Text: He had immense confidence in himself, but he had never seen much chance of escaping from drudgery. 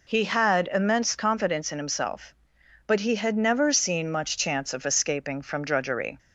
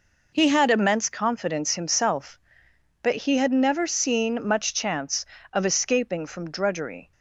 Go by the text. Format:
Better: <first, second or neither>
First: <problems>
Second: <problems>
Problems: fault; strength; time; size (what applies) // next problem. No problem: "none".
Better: first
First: none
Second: skips "in"; at 1.7 s